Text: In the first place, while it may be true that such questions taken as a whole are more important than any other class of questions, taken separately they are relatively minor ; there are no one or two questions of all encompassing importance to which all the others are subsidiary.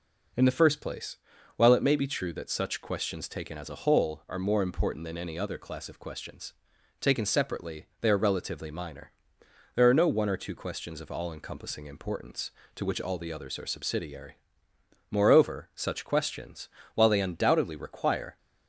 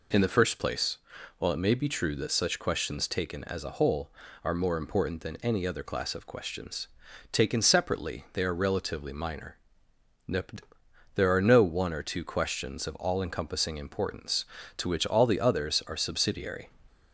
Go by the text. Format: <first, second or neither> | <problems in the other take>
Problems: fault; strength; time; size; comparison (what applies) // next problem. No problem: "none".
second | pauses between "separately" and "they"; slight; at 7.8 s; 0.16 s long // goes on to say "Moreover such questions while they undoubtedly require"; strong; from 15.1 s on; 3.2 s long